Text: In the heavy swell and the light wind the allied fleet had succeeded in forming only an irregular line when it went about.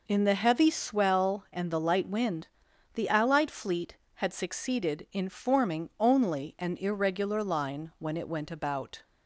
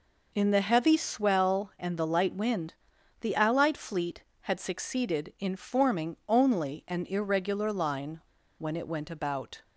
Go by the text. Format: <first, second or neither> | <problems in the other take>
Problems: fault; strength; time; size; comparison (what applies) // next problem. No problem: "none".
first | pauses between "wind" and "the"; noticeable; at 2.7 s; 0.48 s long; noticeable in the first // pauses between "line" and "when"; at 8.2 s; 0.38 s long